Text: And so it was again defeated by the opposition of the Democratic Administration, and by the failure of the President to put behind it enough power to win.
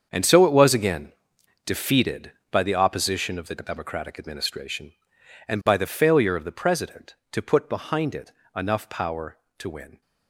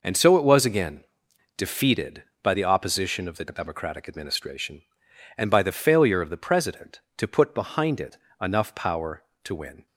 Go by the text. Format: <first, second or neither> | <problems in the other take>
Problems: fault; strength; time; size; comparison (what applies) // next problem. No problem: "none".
second | gets quieter; strong; throughout; 12.5 dB // pauses between "again" and "defeated"; noticeable; at 1.1 s; 0.52 s long; noticeable in the second // pauses between "it" and "enough"; slight; at 8.3 s; 0.22 s long; slight in the second